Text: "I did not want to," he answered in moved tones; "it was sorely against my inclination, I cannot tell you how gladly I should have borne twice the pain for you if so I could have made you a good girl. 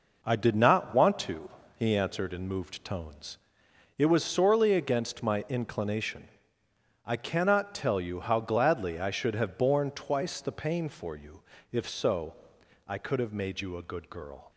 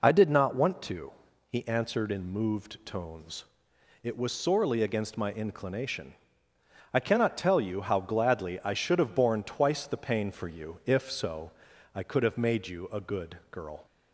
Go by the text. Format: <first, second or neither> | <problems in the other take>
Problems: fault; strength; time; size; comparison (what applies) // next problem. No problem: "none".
second | gets quieter; throughout; 6.5 dB // pauses between "you" and "if"; slight; at 11.4 s; 0.30 s long // pauses between "so" and "I"; noticeable; at 12.3 s; 0.50 s long; also in the second